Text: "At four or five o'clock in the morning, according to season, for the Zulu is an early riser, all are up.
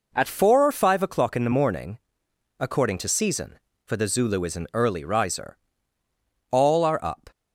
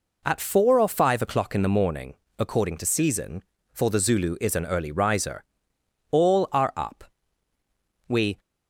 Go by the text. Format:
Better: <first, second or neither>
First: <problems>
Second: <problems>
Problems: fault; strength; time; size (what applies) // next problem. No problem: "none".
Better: first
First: none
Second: goes on to say "We"; slight; from 8.0 s on; 0.32 s long